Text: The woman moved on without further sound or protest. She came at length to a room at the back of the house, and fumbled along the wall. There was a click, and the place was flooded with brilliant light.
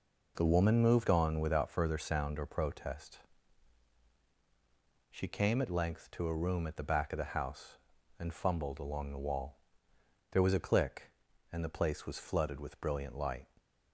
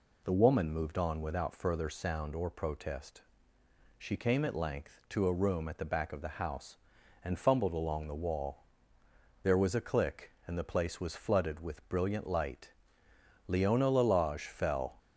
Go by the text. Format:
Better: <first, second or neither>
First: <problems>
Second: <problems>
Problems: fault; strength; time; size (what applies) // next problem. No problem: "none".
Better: first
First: none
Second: goes on to say "Leona Lalage fell"; from 13.4 s on; 1.5 s long